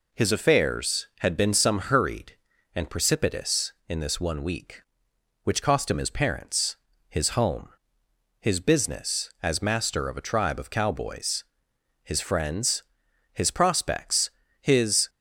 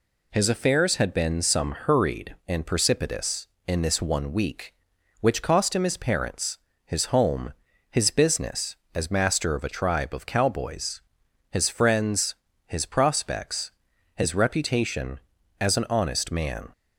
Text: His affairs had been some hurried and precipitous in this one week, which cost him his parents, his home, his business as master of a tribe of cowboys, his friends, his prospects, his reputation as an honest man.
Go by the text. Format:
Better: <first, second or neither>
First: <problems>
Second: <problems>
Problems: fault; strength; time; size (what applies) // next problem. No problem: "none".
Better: second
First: stops before "reputation as an honest man"; at 15.0 s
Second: none